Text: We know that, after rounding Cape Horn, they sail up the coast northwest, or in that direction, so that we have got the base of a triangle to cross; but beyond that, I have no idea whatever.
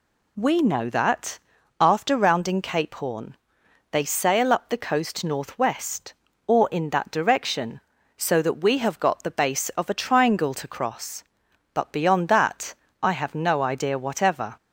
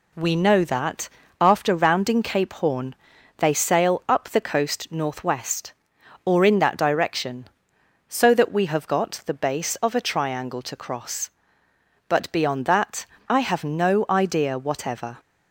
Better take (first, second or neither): neither